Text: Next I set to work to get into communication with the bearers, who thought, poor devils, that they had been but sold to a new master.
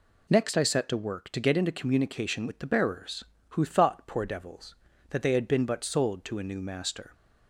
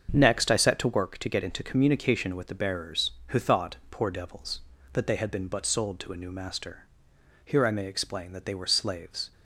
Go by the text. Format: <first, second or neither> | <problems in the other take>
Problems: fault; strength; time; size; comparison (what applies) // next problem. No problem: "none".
first | starts louder than the rest; until 1.1 s; 7 dB // goes on to say "Here I may explain that they were slaves"; strong; from 7.4 s on; 1.8 s long